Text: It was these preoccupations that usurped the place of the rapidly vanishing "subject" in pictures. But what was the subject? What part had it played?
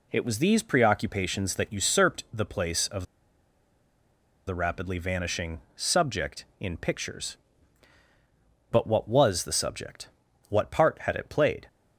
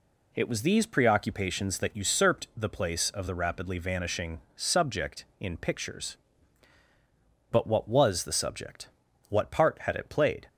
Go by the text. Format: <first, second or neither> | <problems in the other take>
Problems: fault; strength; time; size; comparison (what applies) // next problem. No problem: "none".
second | pauses between "of" and "the"; strong; at 3.0 s; 1.4 s long // pauses between "vanishing" and "subject"; slight; at 5.5 s; 0.16 s long; slight in the second